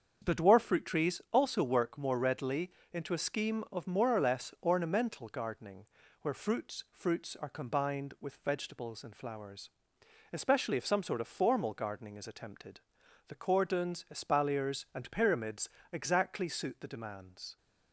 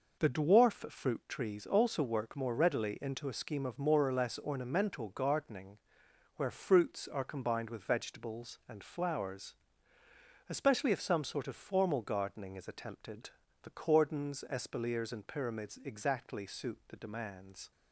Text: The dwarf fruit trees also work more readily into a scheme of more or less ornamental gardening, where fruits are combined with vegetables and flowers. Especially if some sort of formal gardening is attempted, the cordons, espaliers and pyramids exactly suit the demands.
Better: second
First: starts louder than the rest; strong; until 1.3 s; 7 dB // pauses between "readily" and "into"; slight; at 2.7 s; 0.22 s long // says "fruits" twice; at 6.9 s // pauses between "pyramids" and "exactly"; slight; at 15.7 s; 0.20 s long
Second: none

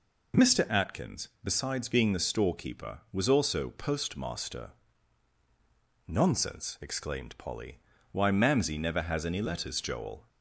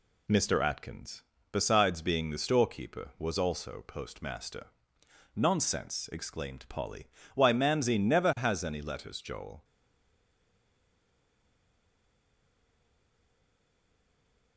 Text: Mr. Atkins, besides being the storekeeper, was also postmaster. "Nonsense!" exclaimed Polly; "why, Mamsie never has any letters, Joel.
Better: first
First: none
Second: stays silent after the last word; strong; from 9.6 s on; 4.9 s long

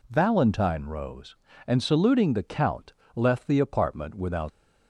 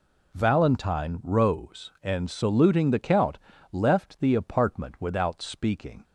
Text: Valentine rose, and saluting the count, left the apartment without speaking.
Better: second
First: stops before "speaking"; at 4.4 s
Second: none

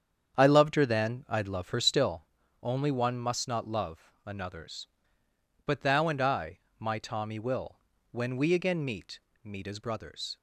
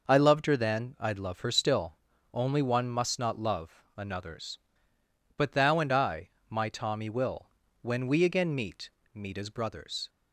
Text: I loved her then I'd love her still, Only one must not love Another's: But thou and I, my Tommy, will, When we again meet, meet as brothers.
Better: second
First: starts louder than the rest; strong; until 2.2 s; 8 dB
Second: none

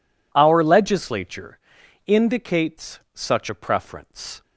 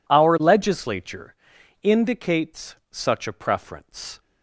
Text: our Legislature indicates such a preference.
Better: neither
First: pauses between "Legislature" and "indicates"; noticeable; at 1.5 s; 0.48 s long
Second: pauses between "Legislature" and "indicates"; noticeable; at 1.3 s; 0.48 s long

